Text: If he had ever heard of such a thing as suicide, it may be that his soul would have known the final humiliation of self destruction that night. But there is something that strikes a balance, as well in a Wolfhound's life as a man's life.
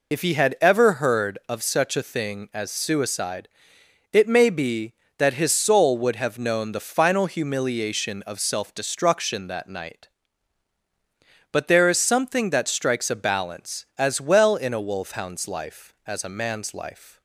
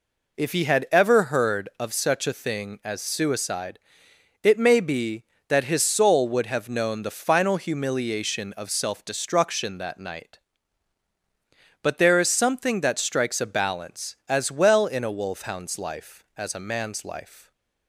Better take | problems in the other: second | loses the start of "If"; at 0.1 s; 50 ms

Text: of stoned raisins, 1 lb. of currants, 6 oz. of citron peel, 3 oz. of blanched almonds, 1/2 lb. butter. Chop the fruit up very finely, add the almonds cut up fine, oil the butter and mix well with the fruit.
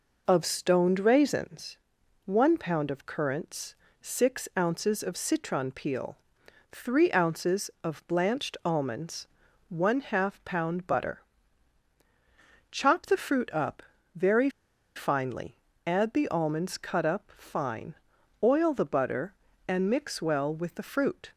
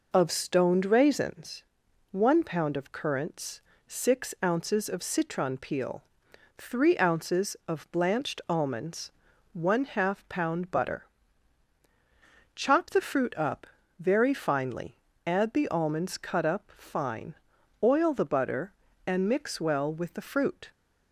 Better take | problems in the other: second | pauses between "up" and "very"; slight; at 13.8 s; 0.34 s long; slight in the second // pauses between "very" and "finely"; noticeable; at 14.4 s; 0.46 s long

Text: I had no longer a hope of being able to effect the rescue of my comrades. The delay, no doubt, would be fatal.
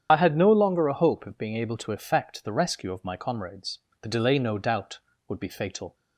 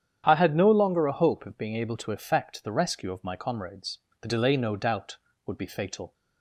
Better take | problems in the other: second | loses the start of "I"; at 0.0 s; 50 ms // starts louder than the rest; strong; until 1.1 s; 9 dB; strong in the second

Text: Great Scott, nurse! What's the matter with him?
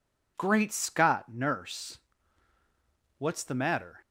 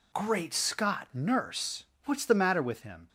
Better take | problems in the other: second | stops before "with him"; at 4.0 s

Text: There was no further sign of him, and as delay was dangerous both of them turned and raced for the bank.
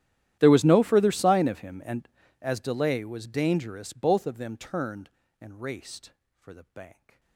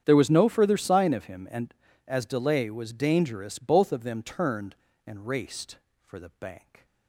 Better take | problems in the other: second | gets quieter; strong; throughout; 30 dB // starts louder than the rest; strong; until 1.4 s; 12 dB; strong in the second

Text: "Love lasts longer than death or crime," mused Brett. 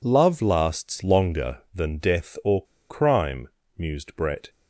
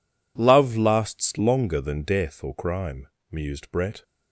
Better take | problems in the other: second | pauses between "or" and "crime"; slight; at 2.6 s; 0.28 s long

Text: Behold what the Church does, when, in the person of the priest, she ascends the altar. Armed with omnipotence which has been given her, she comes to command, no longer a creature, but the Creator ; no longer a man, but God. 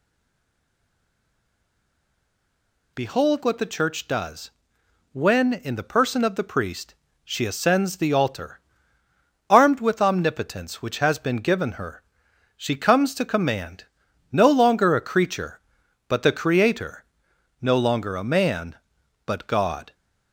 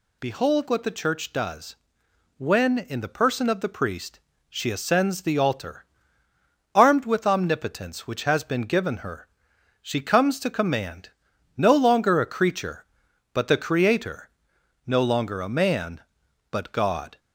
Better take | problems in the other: second | stays silent before the first word; strong; until 2.9 s; 2.9 s long

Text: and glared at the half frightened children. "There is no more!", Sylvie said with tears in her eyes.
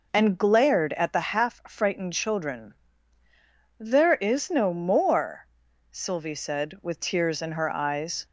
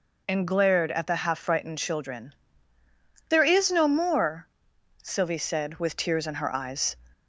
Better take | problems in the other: neither | none

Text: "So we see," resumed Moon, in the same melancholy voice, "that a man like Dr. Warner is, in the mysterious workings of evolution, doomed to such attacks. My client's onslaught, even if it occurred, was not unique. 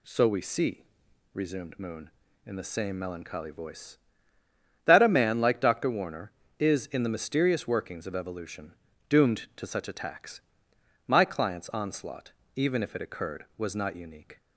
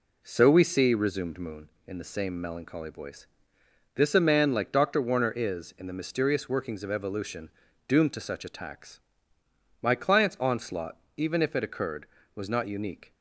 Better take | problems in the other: first | says "this" for "that"; at 3.9 s

